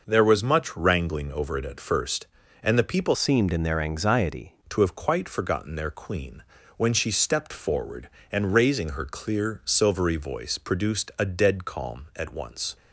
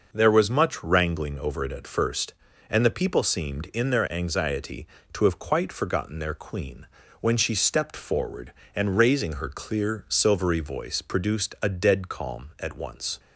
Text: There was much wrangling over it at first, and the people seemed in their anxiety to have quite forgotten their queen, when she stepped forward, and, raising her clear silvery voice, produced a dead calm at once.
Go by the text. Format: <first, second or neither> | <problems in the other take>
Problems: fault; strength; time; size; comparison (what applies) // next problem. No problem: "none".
second | changes voice from "seemed" to "anxiety"; from 3.1 to 4.5 s; 1.4 s long